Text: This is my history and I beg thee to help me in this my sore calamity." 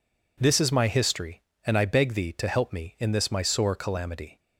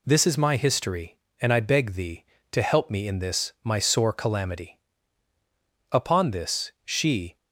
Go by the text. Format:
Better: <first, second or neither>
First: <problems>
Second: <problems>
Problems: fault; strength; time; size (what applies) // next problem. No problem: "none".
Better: first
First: none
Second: goes on to say "Upon this she"; from 5.9 s on; 1.4 s long